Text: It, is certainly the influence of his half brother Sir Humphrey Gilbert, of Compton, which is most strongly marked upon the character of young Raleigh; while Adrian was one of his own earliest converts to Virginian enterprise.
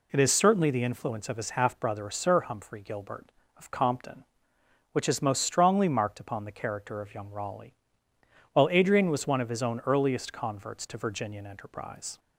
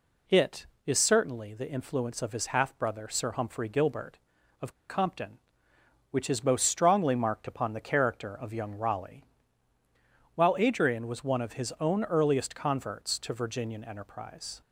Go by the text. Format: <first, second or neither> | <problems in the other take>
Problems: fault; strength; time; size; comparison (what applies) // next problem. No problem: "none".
first | pauses between "of" and "Compton"; slight; at 4.7 s; 0.17 s long